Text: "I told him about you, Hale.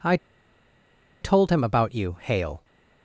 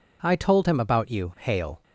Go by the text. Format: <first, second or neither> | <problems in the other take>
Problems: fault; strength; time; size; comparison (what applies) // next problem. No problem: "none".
second | pauses between "I" and "told"; at 0.1 s; 1.0 s long